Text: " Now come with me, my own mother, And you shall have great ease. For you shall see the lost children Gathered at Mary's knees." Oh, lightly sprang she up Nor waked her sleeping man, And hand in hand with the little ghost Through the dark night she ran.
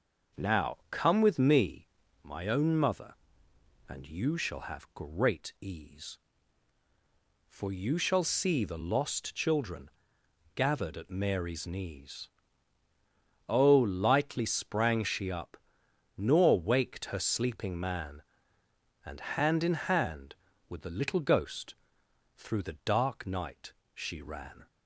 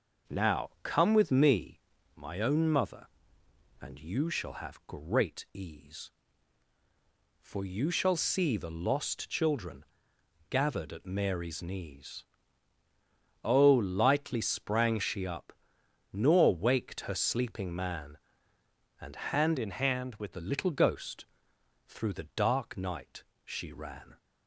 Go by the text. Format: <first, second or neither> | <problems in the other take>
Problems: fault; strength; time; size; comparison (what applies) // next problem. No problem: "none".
first | pauses between "children" and "Gathered"; noticeable; at 9.8 s; 0.66 s long; noticeable in the first // pauses between "up" and "Nor"; noticeable; at 15.5 s; 0.60 s long; noticeable in the first // changes voice from "in" to "with"; from 19.5 to 20.3 s; 0.8 s long // pauses between "ghost" and "Through"; noticeable; at 21.2 s; 0.62 s long; noticeable in the first // pauses between "night" and "she"; slight; at 23.2 s; 0.20 s long; slight in the first